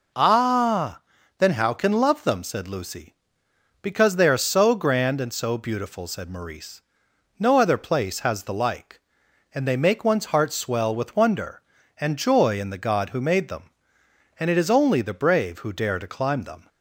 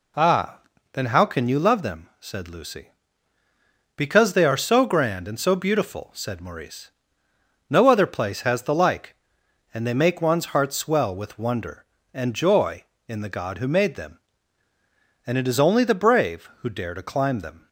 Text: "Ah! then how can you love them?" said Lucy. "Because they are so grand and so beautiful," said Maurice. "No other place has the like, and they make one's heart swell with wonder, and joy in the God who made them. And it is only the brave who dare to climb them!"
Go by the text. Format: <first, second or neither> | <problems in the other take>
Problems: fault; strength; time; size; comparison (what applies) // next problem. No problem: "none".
second | skips "you"; at 1.9 s